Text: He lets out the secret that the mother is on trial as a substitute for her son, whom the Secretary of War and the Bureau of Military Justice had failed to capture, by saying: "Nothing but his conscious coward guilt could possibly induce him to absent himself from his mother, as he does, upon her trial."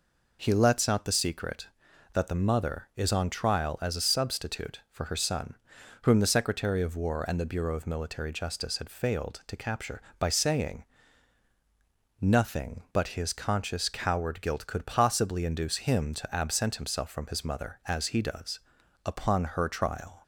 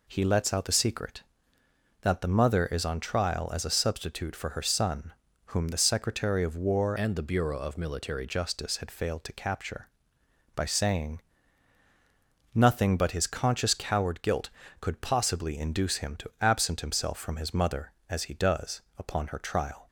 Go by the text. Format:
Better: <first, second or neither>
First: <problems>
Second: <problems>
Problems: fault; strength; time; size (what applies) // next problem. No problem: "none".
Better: first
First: none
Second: changes voice from "and" to "Military"; from 6.9 to 8.2 s; 1.3 s long